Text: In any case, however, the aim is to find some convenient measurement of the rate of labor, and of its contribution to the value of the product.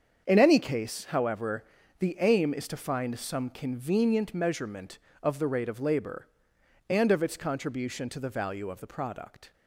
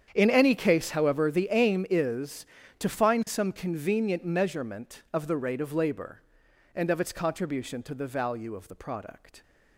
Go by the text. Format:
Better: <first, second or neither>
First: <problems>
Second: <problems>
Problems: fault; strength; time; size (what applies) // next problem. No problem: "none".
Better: neither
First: starts louder than the rest; strong; until 1.2 s; 7 dB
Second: starts louder than the rest; strong; until 1.1 s; 8.5 dB